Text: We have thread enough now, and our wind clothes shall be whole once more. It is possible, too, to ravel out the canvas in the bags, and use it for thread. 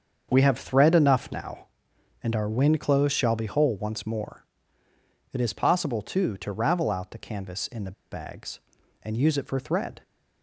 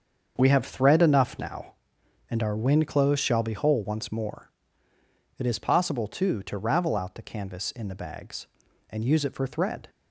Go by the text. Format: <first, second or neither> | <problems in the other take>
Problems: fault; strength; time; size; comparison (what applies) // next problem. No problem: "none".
second | starts louder than the rest; until 1.3 s; 7 dB; also in the second // pauses between "the" and "bags"; slight; at 7.9 s; 0.19 s long